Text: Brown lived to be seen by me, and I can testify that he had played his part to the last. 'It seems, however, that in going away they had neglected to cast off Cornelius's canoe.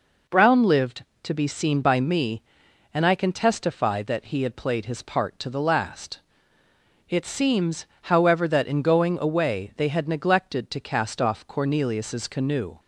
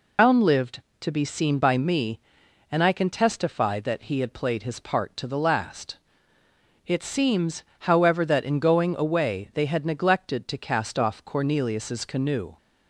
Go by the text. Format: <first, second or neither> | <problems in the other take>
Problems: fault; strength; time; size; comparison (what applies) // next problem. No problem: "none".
first | loses the start of "Brown"; at 0.1 s; 125 ms